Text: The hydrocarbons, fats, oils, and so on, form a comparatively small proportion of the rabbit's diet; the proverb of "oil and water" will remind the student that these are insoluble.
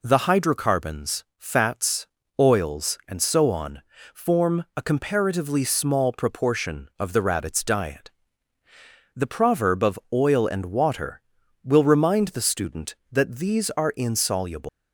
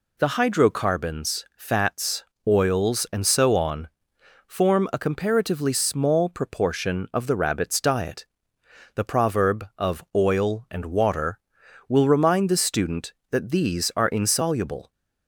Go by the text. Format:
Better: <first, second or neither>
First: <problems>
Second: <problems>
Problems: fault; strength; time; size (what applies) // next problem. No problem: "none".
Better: second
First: leaves "insoluble" unfinished; at 14.6 s; 200 ms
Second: none